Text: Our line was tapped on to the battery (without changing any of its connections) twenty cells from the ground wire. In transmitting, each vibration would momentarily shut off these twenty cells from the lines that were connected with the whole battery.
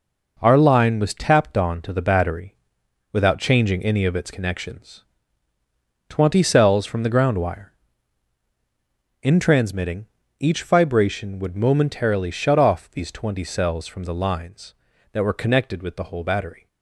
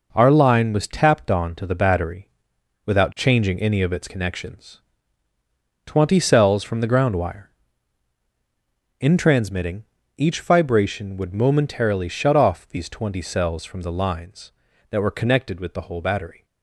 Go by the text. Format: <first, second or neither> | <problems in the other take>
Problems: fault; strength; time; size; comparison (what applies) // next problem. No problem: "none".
neither | none